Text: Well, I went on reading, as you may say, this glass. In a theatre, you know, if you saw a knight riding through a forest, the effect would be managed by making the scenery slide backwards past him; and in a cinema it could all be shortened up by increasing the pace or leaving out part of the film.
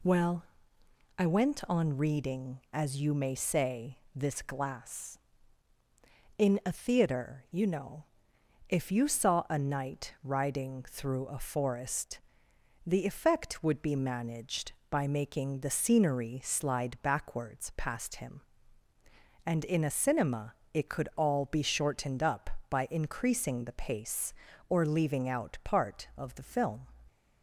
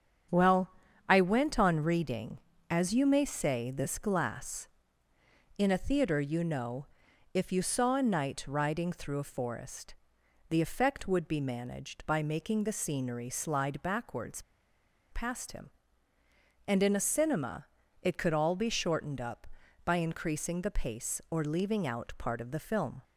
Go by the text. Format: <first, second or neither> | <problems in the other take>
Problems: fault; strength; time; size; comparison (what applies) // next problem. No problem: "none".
first | starts louder than the rest; strong; until 1.7 s; 8 dB // pauses between "backwards" and "past"; noticeable; at 14.4 s; 0.68 s long // pauses between "cinema" and "it"; slight; at 17.6 s; 0.34 s long; slight in the first